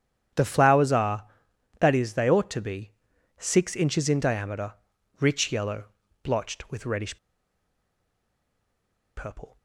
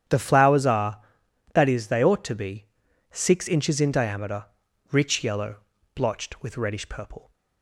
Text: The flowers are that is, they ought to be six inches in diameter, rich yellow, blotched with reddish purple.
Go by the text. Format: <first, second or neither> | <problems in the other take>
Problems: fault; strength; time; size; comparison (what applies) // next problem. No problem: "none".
second | starts louder than the rest; strong; until 1.8 s; 9.5 dB; strong in the second // pauses between "be" and "six"; at 2.9 s; 0.44 s long; also in the second // pauses between "reddish" and "purple"; strong; at 7.1 s; 2.0 s long